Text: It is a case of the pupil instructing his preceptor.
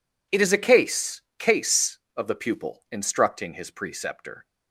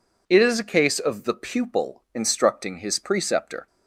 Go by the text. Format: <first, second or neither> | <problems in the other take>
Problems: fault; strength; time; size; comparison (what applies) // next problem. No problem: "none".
second | says "case" twice; at 1.3 s